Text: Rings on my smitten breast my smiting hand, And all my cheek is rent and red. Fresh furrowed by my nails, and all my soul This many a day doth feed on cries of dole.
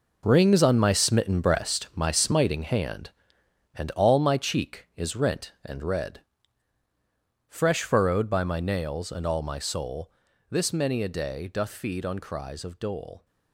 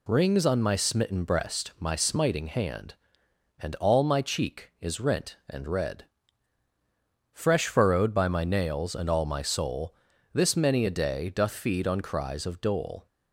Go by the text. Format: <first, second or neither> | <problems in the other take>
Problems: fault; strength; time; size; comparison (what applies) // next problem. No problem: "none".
second | gets quieter; strong; throughout; 11 dB // pauses between "soul" and "This"; at 10.1 s; 0.38 s long; also in the second